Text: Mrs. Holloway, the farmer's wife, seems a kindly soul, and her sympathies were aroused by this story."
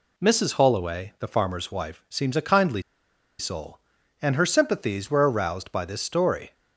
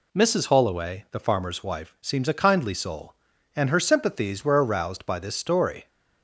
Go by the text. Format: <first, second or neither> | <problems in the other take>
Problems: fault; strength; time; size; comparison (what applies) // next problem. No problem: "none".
second | pauses between "kindly" and "soul"; noticeable; at 2.8 s; 0.58 s long